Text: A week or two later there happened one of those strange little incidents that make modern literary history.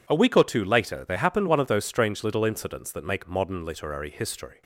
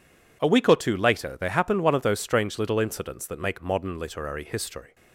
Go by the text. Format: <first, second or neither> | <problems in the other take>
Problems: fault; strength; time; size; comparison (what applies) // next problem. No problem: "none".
neither | none